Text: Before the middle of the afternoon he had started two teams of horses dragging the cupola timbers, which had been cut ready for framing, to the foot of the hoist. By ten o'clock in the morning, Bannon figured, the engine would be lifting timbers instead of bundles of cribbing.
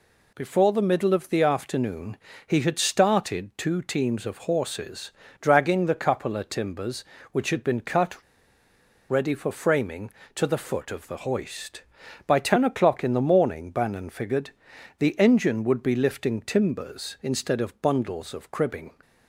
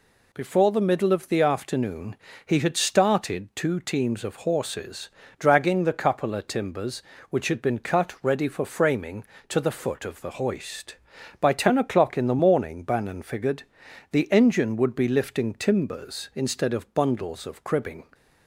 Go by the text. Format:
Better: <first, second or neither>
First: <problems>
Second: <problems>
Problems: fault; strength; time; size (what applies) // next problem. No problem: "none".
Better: second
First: pauses between "afternoon" and "he"; slight; at 2.1 s; 0.30 s long // pauses between "horses" and "dragging"; slight; at 5.1 s; 0.30 s long // pauses between "cut" and "ready"; noticeable; at 8.1 s; 0.92 s long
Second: pauses between "afternoon" and "he"; slight; at 2.1 s; 0.30 s long // pauses between "horses" and "dragging"; slight; at 5.0 s; 0.30 s long